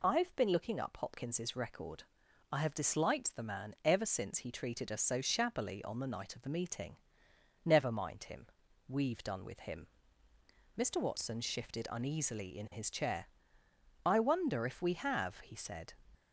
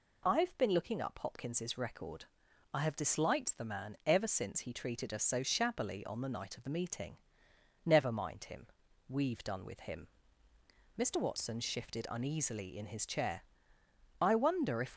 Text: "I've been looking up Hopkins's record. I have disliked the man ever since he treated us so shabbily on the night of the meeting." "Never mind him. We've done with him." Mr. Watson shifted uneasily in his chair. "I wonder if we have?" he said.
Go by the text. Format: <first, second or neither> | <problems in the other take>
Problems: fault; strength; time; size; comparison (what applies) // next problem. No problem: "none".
first | stops before "we have he said"; at 14.9 s